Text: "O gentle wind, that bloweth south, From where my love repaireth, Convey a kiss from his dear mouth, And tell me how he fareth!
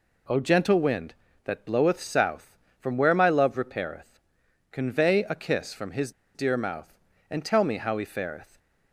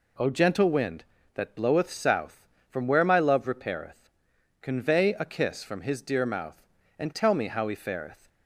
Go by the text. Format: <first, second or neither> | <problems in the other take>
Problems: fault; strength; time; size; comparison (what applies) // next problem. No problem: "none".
second | pauses between "his" and "dear"; slight; at 6.1 s; 0.23 s long